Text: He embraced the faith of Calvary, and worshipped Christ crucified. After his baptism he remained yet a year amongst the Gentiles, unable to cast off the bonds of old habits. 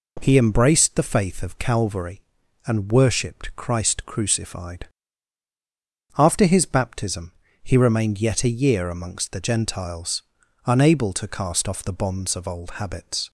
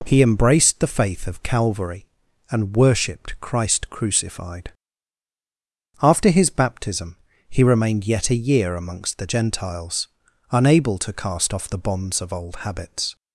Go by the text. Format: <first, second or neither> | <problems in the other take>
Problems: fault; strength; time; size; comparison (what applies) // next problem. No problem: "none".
neither | pauses between "baptism" and "he"; slight; the same in both